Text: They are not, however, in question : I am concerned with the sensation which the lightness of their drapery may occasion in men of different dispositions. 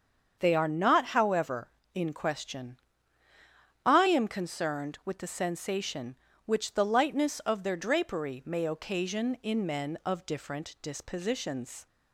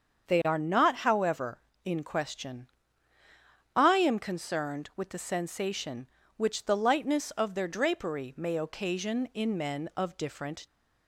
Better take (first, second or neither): first